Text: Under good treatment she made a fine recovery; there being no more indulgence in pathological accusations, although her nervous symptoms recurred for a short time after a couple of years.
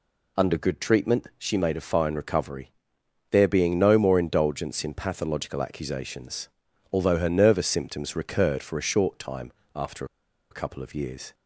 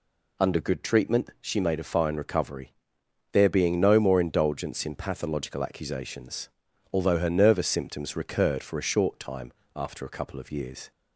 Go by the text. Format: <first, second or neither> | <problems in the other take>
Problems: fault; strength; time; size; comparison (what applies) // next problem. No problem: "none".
second | pauses between "time" and "after"; slight; at 9.5 s; 0.24 s long; slight in the second // pauses between "after" and "a"; noticeable; at 10.0 s; 0.46 s long